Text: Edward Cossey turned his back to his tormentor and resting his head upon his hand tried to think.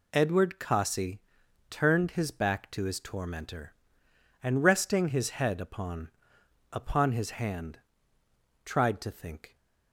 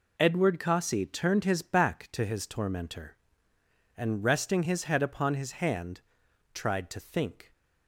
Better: second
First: pauses between "Cossey" and "turned"; noticeable; at 1.2 s; 0.48 s long // says "upon" twice; at 6.7 s // pauses between "hand" and "tried"; noticeable; at 7.7 s; 0.84 s long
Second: pauses between "hand" and "tried"; noticeable; at 6.0 s; 0.52 s long

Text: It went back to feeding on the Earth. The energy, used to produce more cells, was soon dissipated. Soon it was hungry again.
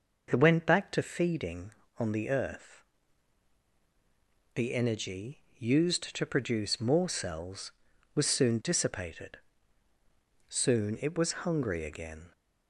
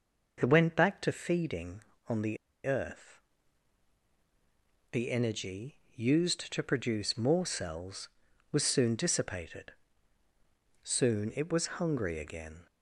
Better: first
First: none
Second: pauses between "the" and "Earth"; slight; at 2.3 s; 0.29 s long

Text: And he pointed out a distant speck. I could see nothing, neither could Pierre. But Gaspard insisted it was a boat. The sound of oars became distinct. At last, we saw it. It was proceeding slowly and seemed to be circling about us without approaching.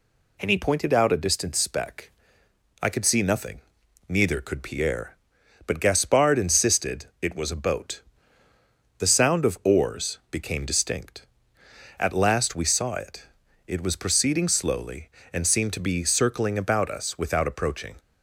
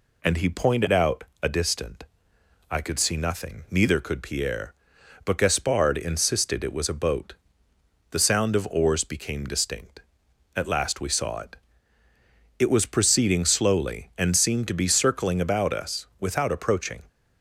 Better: first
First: none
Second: pauses between "out" and "a"; slight; at 1.2 s; 0.18 s long // skips "speck"; at 2.3 s

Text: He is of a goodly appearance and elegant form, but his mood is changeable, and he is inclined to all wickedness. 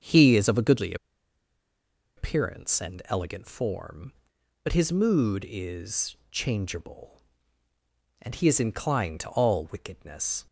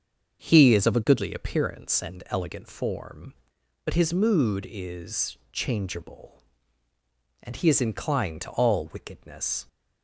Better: second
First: starts louder than the rest; until 2.2 s; 7 dB // pauses between "goodly" and "appearance"; strong; at 0.9 s; 1.2 s long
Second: starts louder than the rest; until 1.5 s; 7 dB

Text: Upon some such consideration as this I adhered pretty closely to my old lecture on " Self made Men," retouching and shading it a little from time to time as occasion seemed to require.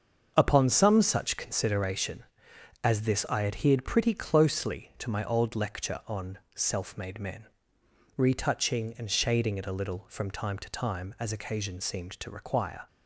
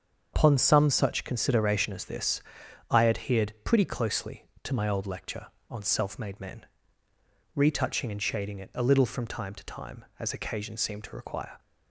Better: first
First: starts louder than the rest; until 1.3 s; 7 dB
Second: loses the start of "Upon"; at 0.3 s; 105 ms // starts louder than the rest; strong; until 1.3 s; 7 dB // pauses between "this" and "I"; noticeable; at 2.4 s; 0.48 s long

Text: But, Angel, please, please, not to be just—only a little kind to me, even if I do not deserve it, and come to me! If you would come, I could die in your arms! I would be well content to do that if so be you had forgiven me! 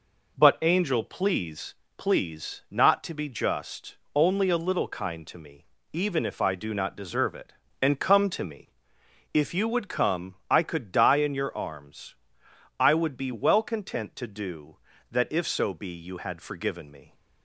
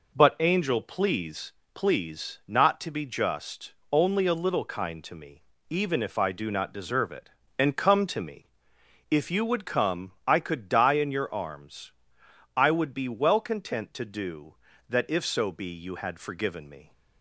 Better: neither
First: none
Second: none

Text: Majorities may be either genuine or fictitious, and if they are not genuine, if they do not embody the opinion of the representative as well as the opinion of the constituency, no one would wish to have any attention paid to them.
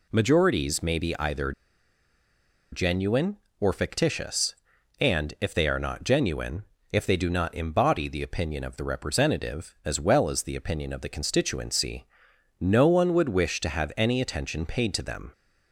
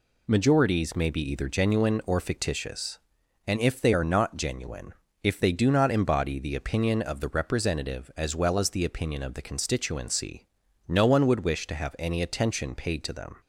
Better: second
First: pauses between "either" and "genuine"; at 1.5 s; 1.2 s long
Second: none

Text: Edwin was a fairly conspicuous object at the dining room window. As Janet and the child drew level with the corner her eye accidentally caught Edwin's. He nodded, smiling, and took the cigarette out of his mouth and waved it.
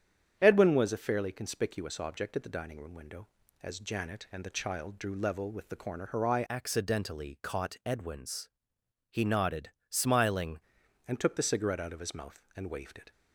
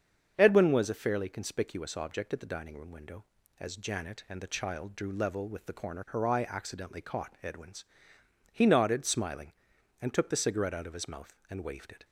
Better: second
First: starts louder than the rest; strong; until 1.4 s; 8.5 dB // changes voice from "accidentally" to "smiling"; from 6.4 to 10.6 s; 4.2 s long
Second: starts louder than the rest; strong; until 1.3 s; 7 dB

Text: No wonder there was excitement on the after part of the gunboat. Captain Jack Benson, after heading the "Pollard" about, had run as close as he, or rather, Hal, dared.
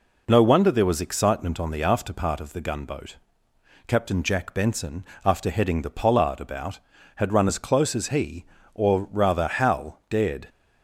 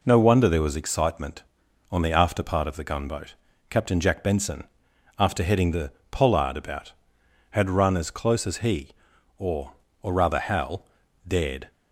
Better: first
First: none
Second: pauses between "the" and "Pollard"; slight; at 5.9 s; 0.20 s long // says "or" twice; at 10.0 s

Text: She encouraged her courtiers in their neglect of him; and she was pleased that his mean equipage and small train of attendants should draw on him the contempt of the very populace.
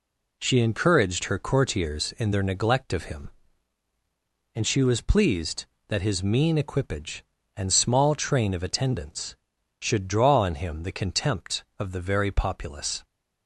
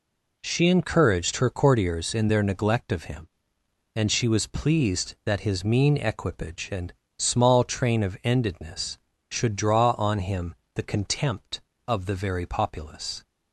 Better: first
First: none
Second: pauses between "and" and "small"; slight; at 6.9 s; 0.24 s long // says "endedness" for "attendants"; at 8.2 s // pauses between "him" and "the"; slight; at 10.5 s; 0.22 s long

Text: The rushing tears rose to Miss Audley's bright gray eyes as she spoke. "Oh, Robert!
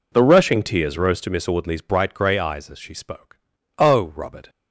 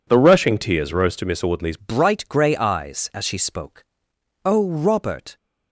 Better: first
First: none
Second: changes voice at "bright"; from 1.7 s on; 3.6 s long

